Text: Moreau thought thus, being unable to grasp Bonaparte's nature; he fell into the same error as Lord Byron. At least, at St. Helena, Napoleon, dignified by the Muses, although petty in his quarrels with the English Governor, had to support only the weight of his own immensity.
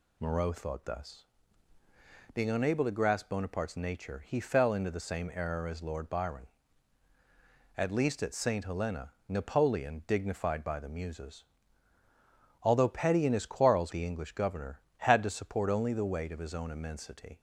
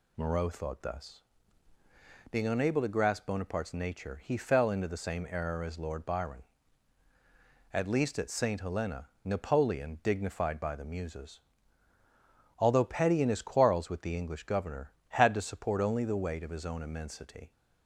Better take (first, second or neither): second